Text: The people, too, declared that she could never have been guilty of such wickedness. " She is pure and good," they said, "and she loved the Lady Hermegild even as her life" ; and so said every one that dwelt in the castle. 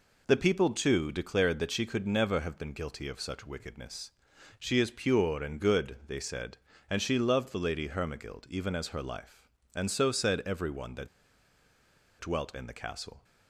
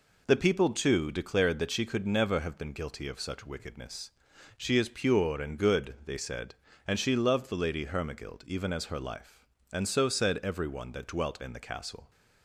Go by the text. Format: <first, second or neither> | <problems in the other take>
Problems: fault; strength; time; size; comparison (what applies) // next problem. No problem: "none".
second | pauses between "that" and "dwelt"; at 11.0 s; 1.1 s long